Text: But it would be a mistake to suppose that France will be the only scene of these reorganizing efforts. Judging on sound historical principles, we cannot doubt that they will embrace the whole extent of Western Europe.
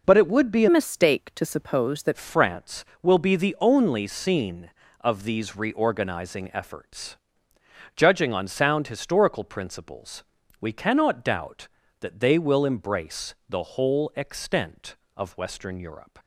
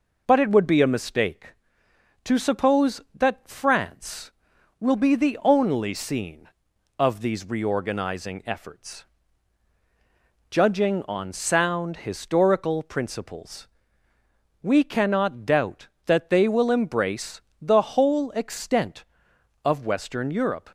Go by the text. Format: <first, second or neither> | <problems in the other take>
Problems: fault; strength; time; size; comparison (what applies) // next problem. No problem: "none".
second | changes voice from "mistake" to "that"; from 0.6 to 2.1 s; 1.5 s long // pauses between "embrace" and "the"; slight; at 13.3 s; 0.16 s long; slight in the second